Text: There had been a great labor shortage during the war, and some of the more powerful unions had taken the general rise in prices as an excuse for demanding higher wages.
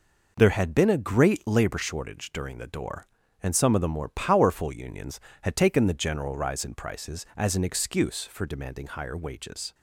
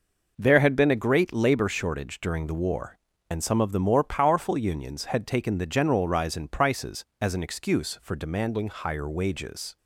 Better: second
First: says "door" for "war"; at 2.6 s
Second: none

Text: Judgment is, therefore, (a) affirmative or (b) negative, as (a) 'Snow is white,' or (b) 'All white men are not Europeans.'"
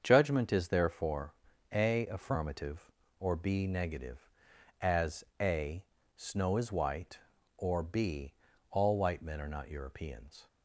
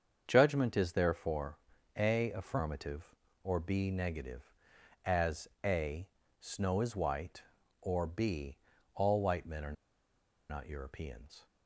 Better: first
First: starts louder than the rest; until 1.0 s; 7 dB // pauses between "as" and "a"; slight; at 5.2 s; 0.18 s long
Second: starts louder than the rest; until 1.2 s; 7 dB // pauses between "as" and "a"; slight; at 5.4 s; 0.18 s long // pauses between "are" and "not"; noticeable; at 9.7 s; 0.76 s long

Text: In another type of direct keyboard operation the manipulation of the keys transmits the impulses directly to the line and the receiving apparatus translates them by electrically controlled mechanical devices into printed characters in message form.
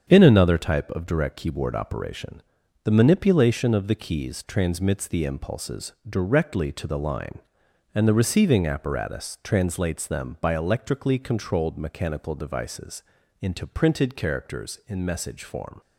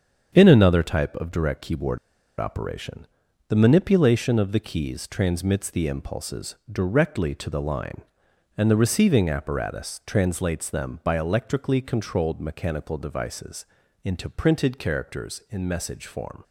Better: first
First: starts louder than the rest; strong; until 1.1 s; 7.5 dB // pauses between "operation" and "the"; at 2.4 s; 0.44 s long // pauses between "impulses" and "directly"; slight; at 5.9 s; 0.16 s long // pauses between "devices" and "into"; slight; at 13.0 s; 0.36 s long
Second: starts louder than the rest; strong; until 1.3 s; 7.5 dB // pauses between "keyboard" and "operation"; at 1.9 s; 0.40 s long // pauses between "operation" and "the"; at 3.0 s; 0.44 s long // pauses between "impulses" and "directly"; slight; at 6.5 s; 0.16 s long // pauses between "devices" and "into"; slight; at 13.6 s; 0.36 s long

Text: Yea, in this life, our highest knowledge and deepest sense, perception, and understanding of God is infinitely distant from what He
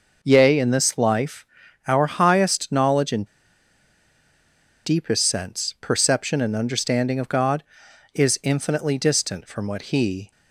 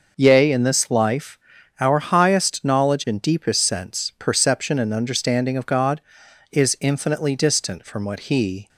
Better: second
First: pauses between "and" and "deepest"; strong; at 3.2 s; 1.5 s long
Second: none

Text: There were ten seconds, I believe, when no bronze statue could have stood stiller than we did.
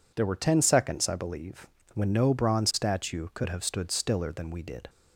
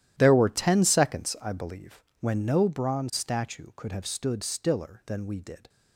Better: first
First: none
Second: gets quieter; strong; throughout; 16 dB

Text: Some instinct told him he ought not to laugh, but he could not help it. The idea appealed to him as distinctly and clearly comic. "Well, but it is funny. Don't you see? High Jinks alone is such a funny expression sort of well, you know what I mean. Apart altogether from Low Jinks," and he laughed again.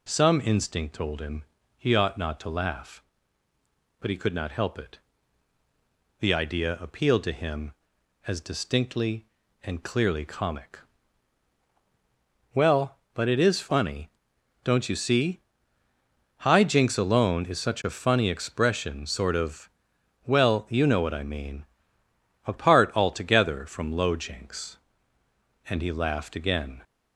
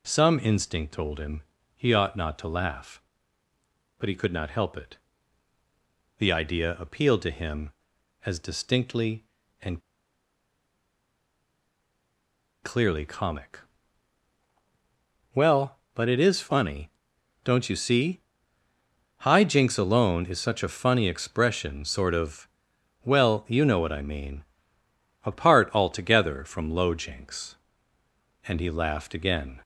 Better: first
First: pauses between "him" and "he"; slight; at 1.4 s; 0.34 s long // pauses between "of" and "well"; noticeable; at 19.6 s; 0.56 s long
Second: pauses between "him" and "he"; slight; at 1.4 s; 0.34 s long // pauses between "and" and "clearly"; strong; at 9.8 s; 2.8 s long // pauses between "of" and "well"; noticeable; at 22.4 s; 0.56 s long

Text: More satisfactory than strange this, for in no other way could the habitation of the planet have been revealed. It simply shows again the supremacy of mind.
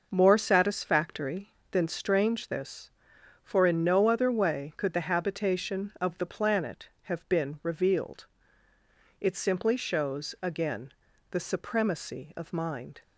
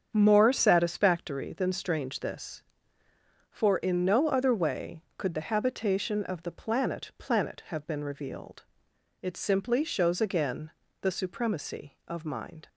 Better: first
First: pauses between "again" and "the"; at 10.9 s; 0.40 s long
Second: starts louder than the rest; strong; until 1.1 s; 7.5 dB // says "planet" twice; at 7.1 s // pauses between "again" and "the"; slight; at 10.7 s; 0.30 s long

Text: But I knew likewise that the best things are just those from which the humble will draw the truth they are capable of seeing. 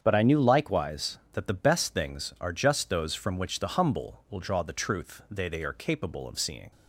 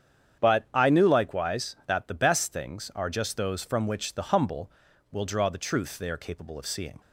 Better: second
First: starts louder than the rest; strong; until 1.0 s; 8 dB // says "they" twice; at 5.4 s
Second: starts louder than the rest; strong; until 1.4 s; 8.5 dB

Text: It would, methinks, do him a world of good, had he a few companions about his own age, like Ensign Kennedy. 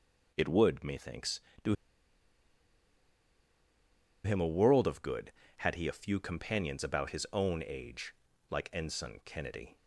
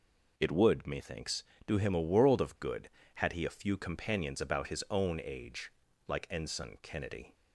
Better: second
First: pauses between "do" and "him"; strong; at 1.7 s; 2.4 s long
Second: none

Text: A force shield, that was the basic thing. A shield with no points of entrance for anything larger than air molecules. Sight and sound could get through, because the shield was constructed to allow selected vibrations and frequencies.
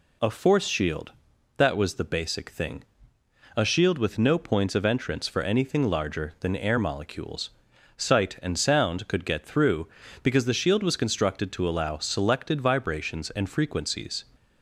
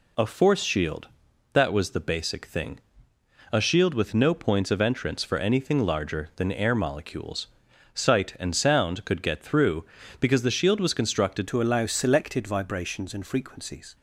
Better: first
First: none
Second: changes voice at "to"; from 11.4 s on; 2.5 s long

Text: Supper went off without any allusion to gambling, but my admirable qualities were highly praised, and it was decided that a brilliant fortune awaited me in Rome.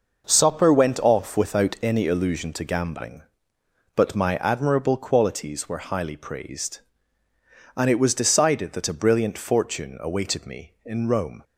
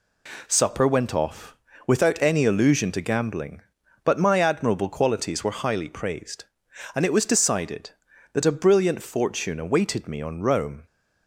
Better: first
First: none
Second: pauses between "off" and "without"; slight; at 1.5 s; 0.32 s long // says "on" for "in"; at 10.2 s

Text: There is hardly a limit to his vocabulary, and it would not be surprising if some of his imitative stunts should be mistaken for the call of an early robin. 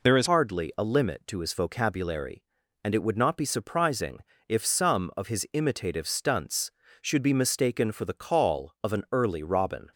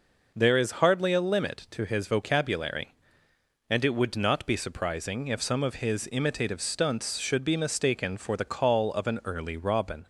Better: second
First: changes voice at "hardly"; from 0.2 s on; 9.7 s long // pauses between "surprising" and "if"; slight; at 4.1 s; 0.28 s long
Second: none

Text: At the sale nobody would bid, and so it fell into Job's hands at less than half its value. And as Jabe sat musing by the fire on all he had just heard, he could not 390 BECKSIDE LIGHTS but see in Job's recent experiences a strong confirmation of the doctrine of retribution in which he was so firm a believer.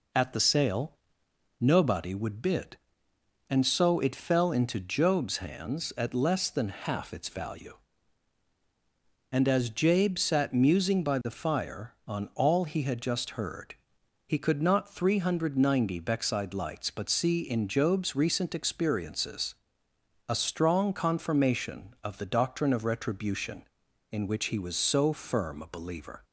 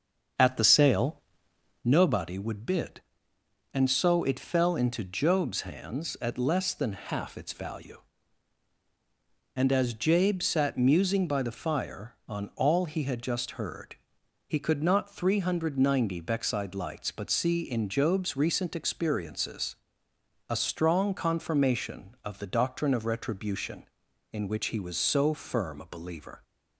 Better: first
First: pauses between "sale" and "nobody"; noticeable; at 0.9 s; 0.64 s long // pauses between "experiences" and "a"; noticeable; at 19.5 s; 0.72 s long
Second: starts louder than the rest; until 1.9 s; 7 dB // pauses between "sale" and "nobody"; noticeable; at 1.2 s; 0.64 s long // pauses between "experiences" and "a"; noticeable; at 19.7 s; 0.72 s long

